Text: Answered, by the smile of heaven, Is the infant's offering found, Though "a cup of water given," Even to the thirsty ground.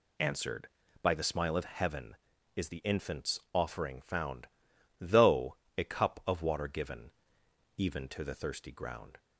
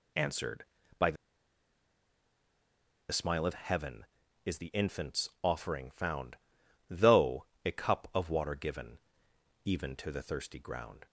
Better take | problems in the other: first | pauses between "the" and "smile"; strong; at 1.1 s; 1.9 s long // pauses between "Though" and "a"; slight; at 7.4 s; 0.18 s long; slight in the first

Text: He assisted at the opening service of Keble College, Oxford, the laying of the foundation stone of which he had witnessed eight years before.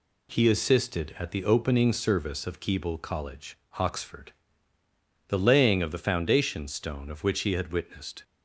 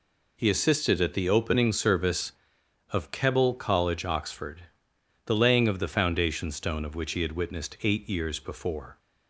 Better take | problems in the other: second | stops before "eight years before"; at 8.2 s

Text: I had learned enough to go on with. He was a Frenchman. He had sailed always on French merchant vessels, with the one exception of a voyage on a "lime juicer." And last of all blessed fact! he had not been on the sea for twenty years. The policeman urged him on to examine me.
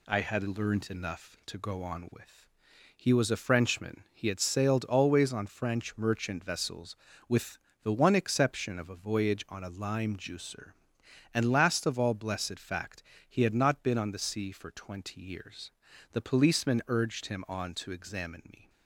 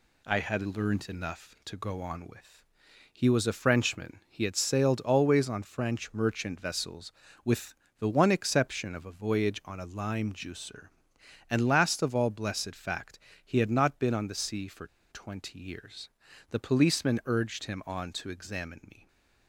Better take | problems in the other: first | pauses between "with" and "the"; slight; at 7.7 s; 0.26 s long; slight in the first // pauses between "for" and "twenty"; slight; at 14.8 s; 0.25 s long

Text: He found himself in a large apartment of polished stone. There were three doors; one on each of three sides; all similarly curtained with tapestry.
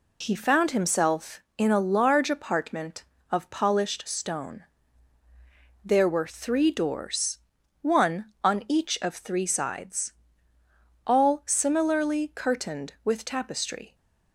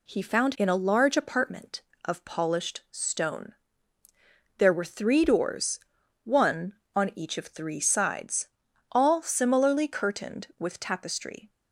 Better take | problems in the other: first | skips "himself"; at 0.5 s

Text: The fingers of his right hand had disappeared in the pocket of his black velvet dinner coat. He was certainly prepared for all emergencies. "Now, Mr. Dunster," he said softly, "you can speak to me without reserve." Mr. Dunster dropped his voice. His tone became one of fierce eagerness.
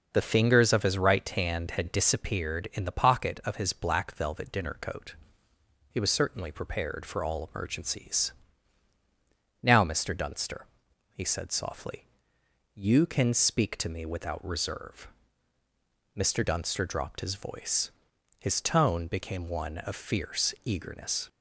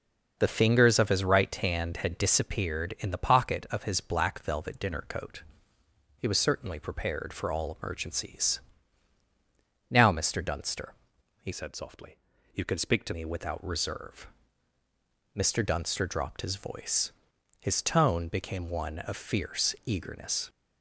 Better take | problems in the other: first | starts louder than the rest; noticeable; until 1.4 s; 6 dB // changes voice from "said" to "to"; from 11.5 to 13.1 s; 1.6 s long

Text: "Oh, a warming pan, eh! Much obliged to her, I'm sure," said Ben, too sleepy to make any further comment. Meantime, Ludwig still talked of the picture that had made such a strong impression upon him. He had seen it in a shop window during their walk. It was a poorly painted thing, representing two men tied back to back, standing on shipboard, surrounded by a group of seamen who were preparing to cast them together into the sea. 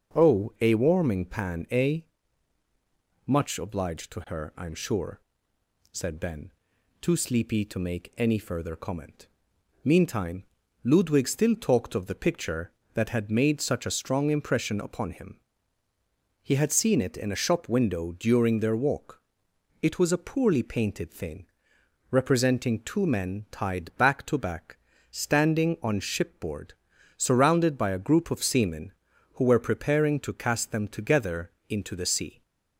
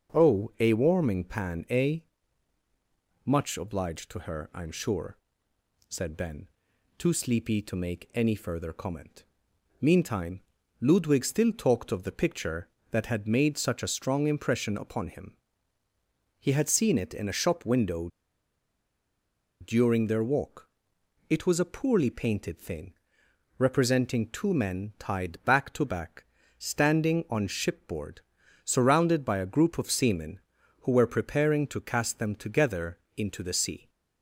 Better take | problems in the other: first | starts louder than the rest; noticeable; until 1.2 s; 6 dB; noticeable in the first // pauses between "window" and "during"; strong; at 18.0 s; 1.5 s long // pauses between "together" and "into"; slight; at 32.9 s; 0.18 s long; slight in the first

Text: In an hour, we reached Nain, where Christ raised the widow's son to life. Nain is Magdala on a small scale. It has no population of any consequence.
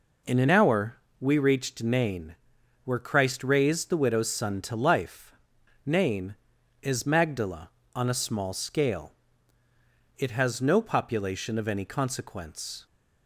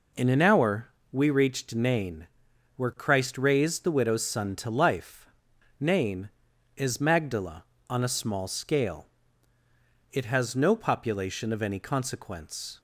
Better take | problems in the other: neither | none

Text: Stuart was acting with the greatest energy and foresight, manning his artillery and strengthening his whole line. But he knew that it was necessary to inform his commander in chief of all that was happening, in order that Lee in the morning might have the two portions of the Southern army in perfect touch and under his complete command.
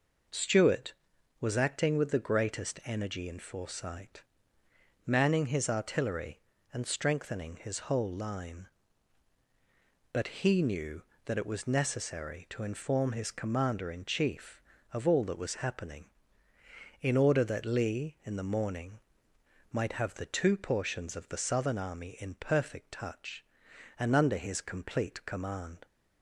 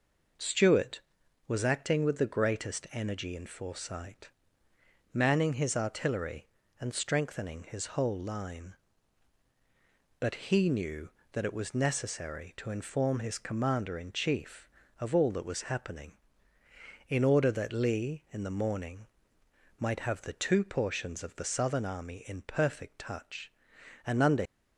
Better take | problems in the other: first | pauses between "morning" and "might"; noticeable; at 19.0 s; 0.72 s long; noticeable in the first // stops before "his complete command"; at 24.4 s

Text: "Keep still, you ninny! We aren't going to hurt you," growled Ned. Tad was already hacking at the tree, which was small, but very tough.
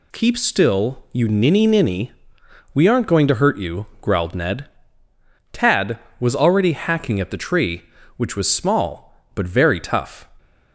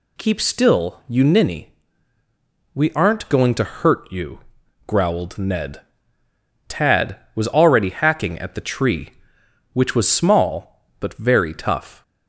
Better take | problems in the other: second | says "ninny" twice; at 1.6 s

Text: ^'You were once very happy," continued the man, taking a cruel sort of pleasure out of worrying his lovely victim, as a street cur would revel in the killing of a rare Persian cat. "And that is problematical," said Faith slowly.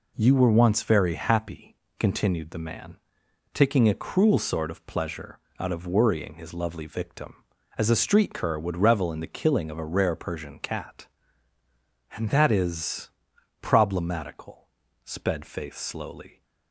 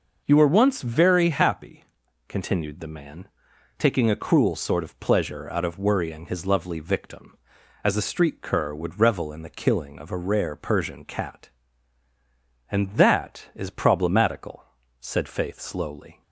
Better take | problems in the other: second | pauses between "pleasure" and "out"; slight; at 5.3 s; 0.20 s long // pauses between "is" and "problematical"; noticeable; at 13.0 s; 0.52 s long // says "sped" for "said"; at 15.0 s

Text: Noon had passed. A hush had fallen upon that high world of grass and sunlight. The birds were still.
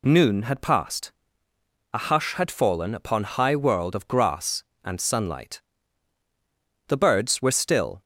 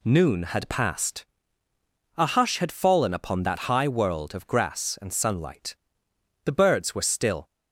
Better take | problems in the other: second | skips "that"; at 3.2 s

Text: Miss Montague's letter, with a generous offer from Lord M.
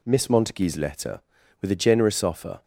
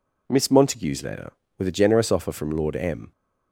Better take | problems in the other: second | stops before "from Lord M"; at 2.6 s

